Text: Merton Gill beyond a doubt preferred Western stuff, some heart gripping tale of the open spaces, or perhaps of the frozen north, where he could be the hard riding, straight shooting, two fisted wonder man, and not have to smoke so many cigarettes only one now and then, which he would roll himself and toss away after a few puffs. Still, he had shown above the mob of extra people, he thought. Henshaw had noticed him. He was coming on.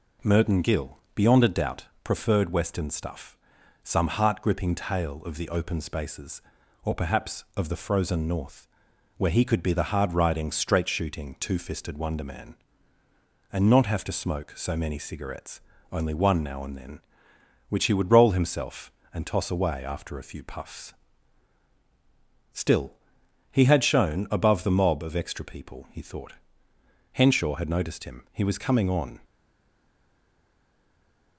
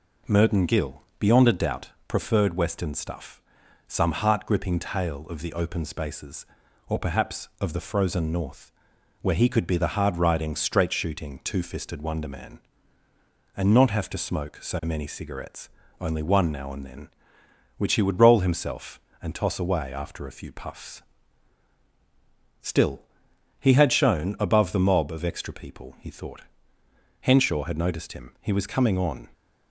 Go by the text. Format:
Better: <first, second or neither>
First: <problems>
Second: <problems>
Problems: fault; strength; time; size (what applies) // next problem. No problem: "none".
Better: second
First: pauses between "Gill" and "beyond"; slight; at 0.9 s; 0.16 s long // pauses between "doubt" and "preferred"; slight; at 1.8 s; 0.18 s long // pauses between "cigarettes" and "only"; slight; at 15.5 s; 0.32 s long // stays silent after the last word; from 29.2 s on; 2.1 s long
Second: pauses between "Gill" and "beyond"; slight; at 1.0 s; 0.16 s long // pauses between "doubt" and "preferred"; slight; at 1.8 s; 0.18 s long // pauses between "cigarettes" and "only"; slight; at 15.6 s; 0.32 s long